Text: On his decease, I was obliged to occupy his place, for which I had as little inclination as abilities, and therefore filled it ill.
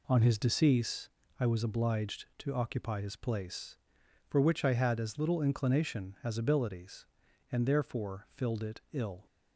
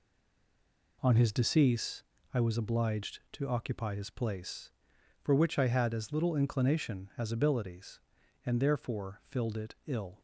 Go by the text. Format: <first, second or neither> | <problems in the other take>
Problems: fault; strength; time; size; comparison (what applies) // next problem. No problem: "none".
first | stays silent before the first word; until 0.9 s; 0.9 s long